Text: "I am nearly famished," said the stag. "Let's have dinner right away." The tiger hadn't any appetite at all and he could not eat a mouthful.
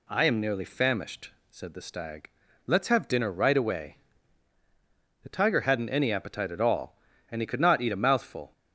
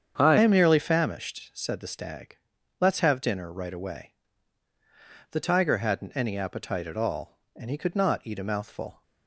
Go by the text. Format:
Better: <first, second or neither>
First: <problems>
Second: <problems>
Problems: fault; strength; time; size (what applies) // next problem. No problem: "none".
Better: first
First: none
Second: starts louder than the rest; strong; until 1.2 s; 7.5 dB // changes voice at "am"; from 0.3 s on; 8.7 s long